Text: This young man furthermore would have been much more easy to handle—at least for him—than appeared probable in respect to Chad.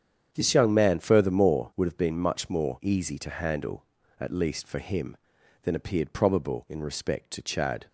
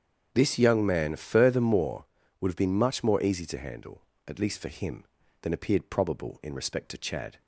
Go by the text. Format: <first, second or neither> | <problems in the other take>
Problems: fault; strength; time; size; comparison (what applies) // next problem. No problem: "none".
neither | starts louder than the rest; strong; the same in both